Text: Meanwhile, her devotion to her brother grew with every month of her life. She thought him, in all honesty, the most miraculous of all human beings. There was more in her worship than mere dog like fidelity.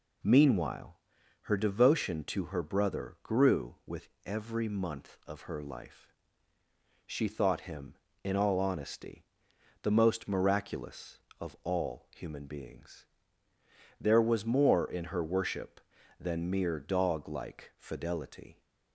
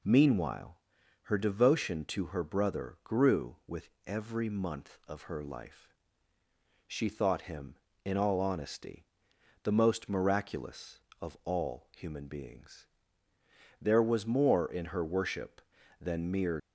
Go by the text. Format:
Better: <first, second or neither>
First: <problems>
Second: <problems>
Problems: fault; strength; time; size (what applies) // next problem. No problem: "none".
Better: first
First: pauses between "with" and "every"; slight; at 4.0 s; 0.18 s long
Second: pauses between "with" and "every"; slight; at 3.8 s; 0.18 s long // stops before "dog like fidelity"; at 16.5 s